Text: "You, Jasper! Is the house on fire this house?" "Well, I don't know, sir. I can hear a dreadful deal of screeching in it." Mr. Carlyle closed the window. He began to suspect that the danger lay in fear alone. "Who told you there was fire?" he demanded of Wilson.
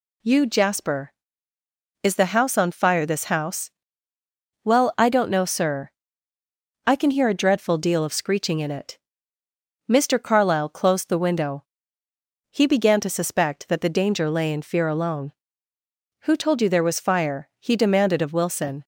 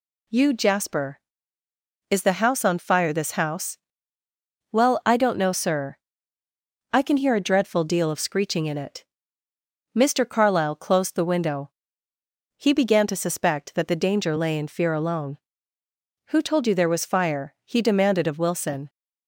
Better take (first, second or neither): neither